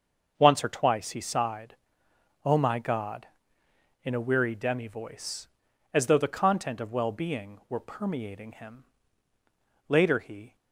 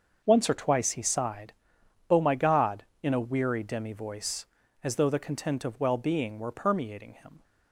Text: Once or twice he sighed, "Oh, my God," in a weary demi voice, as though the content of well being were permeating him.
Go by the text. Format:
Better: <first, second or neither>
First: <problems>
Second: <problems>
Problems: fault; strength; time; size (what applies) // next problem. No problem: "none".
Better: second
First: starts louder than the rest; until 1.4 s; 6.5 dB // goes on to say "Later he"; noticeable; from 9.8 s on; 0.68 s long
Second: starts louder than the rest; until 1.2 s; 6.5 dB